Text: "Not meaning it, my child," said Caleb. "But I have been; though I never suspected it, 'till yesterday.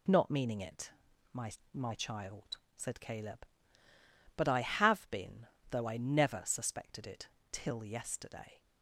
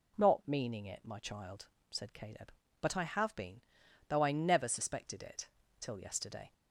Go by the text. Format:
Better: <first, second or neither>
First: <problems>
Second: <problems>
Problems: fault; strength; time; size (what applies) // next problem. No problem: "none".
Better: second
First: says "my" twice; at 1.7 s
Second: none